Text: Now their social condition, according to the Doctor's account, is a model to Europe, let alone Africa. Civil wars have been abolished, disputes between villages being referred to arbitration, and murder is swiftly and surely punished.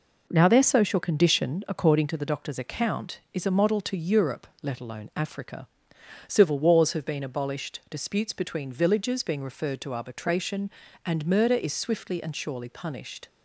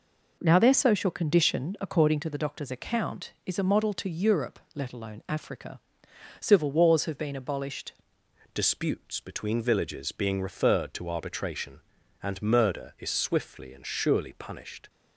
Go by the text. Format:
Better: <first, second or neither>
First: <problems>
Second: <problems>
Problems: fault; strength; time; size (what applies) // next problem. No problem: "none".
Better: first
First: none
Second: changes voice at "disputes"; from 8.5 s on; 6.3 s long